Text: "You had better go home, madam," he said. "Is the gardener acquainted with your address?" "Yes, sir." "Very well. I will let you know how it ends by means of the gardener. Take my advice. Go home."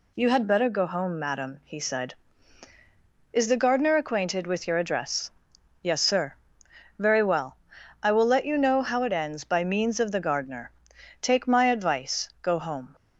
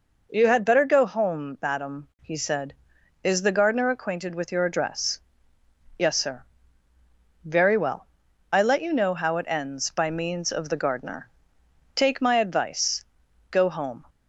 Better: first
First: none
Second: skips "will"; at 8.6 s

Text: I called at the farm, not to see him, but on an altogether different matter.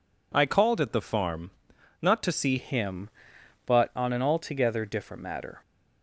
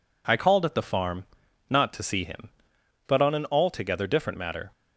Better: second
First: changes voice at "him"; from 2.5 s on; 3.1 s long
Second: none

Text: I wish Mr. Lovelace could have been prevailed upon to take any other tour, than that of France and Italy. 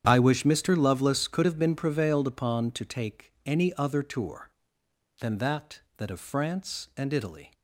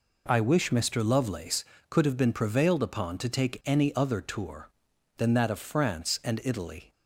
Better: second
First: starts louder than the rest; strong; until 1.0 s; 9 dB // says "that" twice; at 5.9 s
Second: none

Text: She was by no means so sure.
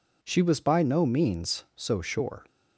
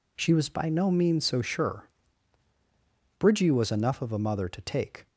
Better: first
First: none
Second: goes on to say "Bridgie was enough of a mother to take"; strong; from 3.1 s on; 1.8 s long

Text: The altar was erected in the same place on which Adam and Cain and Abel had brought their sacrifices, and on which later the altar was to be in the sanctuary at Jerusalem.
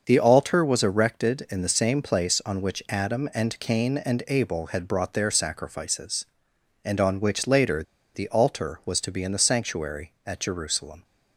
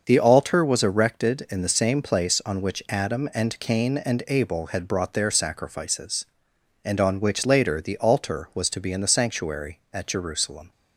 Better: second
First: starts louder than the rest; until 1.0 s; 6.5 dB // pauses between "later" and "the"; slight; at 7.8 s; 0.31 s long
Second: starts louder than the rest; until 1.0 s; 6.5 dB

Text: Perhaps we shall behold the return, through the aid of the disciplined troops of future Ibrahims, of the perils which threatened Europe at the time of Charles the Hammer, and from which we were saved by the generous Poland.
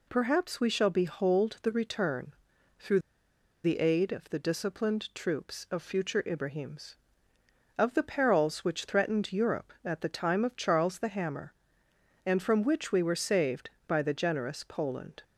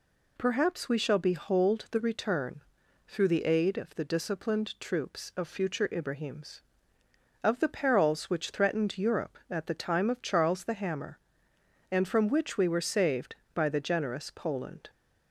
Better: second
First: pauses between "through" and "the"; noticeable; at 2.9 s; 0.64 s long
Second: none

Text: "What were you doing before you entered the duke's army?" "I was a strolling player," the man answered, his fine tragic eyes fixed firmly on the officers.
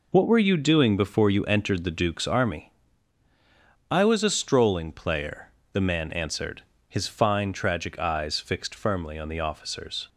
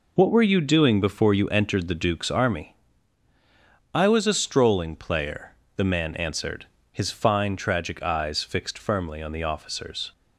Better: neither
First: none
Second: none

